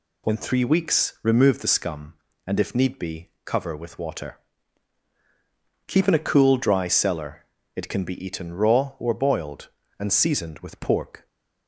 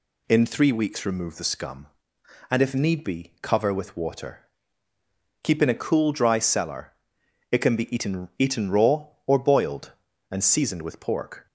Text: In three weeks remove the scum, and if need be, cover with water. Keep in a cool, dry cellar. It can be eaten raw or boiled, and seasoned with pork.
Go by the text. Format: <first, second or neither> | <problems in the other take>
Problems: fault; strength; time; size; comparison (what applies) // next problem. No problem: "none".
first | says "eaten" twice; at 8.3 s